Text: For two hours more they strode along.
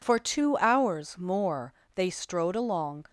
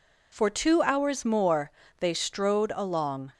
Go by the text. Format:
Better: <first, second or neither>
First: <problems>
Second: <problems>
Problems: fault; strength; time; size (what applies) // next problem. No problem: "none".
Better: neither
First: pauses between "more" and "they"; slight; at 1.7 s; 0.22 s long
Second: pauses between "more" and "they"; slight; at 1.7 s; 0.28 s long